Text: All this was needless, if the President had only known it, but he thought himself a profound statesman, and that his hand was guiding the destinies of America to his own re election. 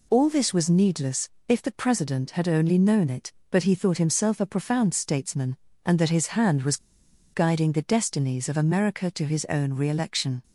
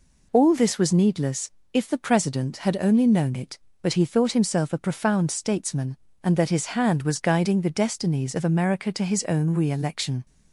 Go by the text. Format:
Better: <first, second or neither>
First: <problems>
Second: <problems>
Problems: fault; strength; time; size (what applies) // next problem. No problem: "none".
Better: second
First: pauses between "was" and "guiding"; noticeable; at 6.7 s; 0.57 s long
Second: none